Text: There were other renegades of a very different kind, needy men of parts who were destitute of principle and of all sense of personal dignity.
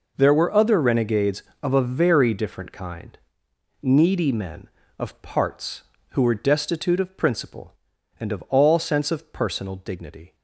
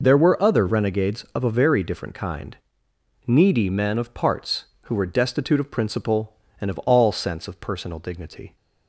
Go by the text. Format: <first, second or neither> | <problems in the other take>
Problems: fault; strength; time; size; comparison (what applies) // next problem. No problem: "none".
neither | none